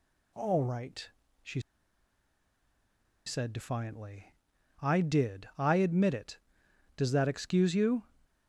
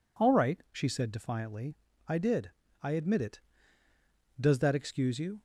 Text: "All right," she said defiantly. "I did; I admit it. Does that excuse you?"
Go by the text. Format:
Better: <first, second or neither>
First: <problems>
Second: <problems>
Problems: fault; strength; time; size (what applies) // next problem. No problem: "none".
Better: second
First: pauses between "she" and "said"; strong; at 1.6 s; 1.6 s long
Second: none